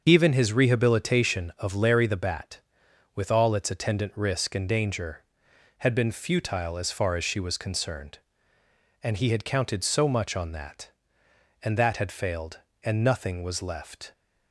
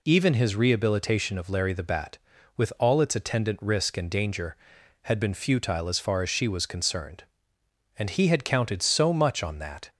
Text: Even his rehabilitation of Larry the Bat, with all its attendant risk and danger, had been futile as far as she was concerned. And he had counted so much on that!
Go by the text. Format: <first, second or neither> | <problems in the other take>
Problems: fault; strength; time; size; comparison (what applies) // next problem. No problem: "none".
second | starts louder than the rest; until 1.0 s; 6.5 dB // goes on to say "And that had failed and nothing was left"; strong; from 11.6 s on; 2.5 s long